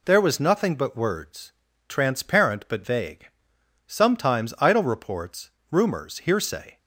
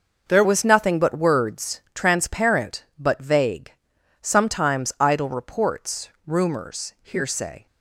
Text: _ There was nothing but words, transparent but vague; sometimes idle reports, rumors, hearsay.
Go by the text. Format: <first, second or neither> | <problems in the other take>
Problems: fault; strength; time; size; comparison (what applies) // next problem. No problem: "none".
first | changes voice at "was"; from 0.4 s on; 7.2 s long